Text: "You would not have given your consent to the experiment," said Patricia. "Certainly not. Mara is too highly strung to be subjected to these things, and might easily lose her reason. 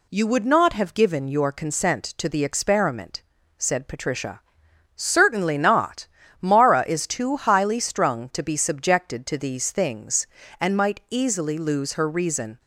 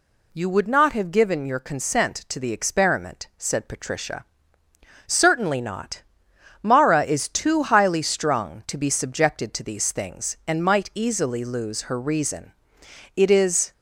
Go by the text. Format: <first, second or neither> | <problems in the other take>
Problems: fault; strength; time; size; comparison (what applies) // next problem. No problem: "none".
first | goes on to say "It is"; from 13.1 s on; 0.56 s long